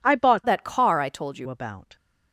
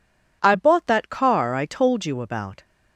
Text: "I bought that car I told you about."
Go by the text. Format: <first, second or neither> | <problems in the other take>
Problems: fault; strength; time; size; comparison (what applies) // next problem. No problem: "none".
second | changes voice from "that" to "you"; from 0.4 to 1.4 s; 1.0 s long